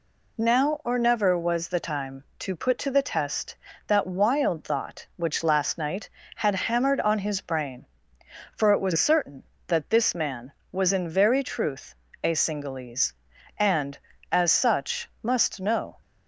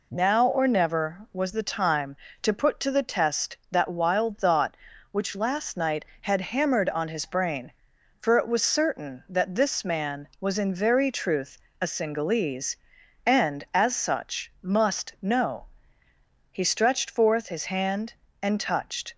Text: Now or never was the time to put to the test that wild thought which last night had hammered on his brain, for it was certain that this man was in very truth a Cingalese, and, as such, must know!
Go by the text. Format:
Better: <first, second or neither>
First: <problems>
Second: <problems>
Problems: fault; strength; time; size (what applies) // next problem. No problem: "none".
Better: first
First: pauses between "truth" and "a"; slight; at 11.9 s; 0.30 s long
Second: pauses between "truth" and "a"; slight; at 11.5 s; 0.24 s long // goes on to say "He stretched forth his hand and touched"; strong; from 16.5 s on; 2.6 s long